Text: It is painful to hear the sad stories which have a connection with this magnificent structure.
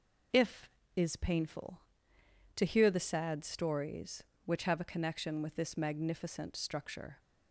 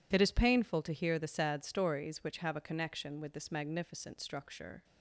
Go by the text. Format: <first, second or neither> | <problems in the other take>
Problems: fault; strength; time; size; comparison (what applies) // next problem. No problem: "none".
second | says "If" for "It"; at 0.3 s